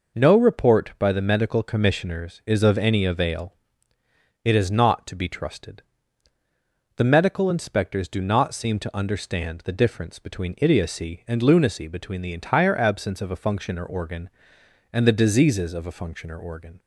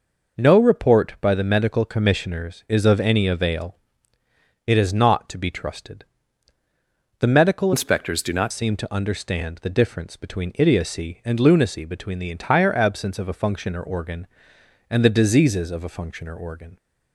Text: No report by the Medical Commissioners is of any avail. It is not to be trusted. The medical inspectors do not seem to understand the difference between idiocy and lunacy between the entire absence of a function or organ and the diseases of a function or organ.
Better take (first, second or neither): first